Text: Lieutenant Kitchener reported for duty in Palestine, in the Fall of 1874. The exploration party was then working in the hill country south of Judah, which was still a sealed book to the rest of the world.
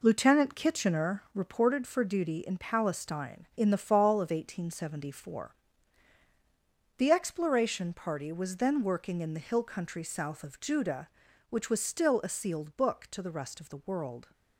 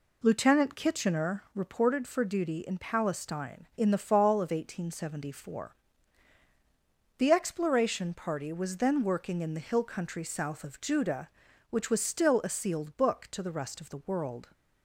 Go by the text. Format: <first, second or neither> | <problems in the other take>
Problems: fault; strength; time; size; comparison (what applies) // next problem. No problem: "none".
second | gets quieter; noticeable; throughout; 6 dB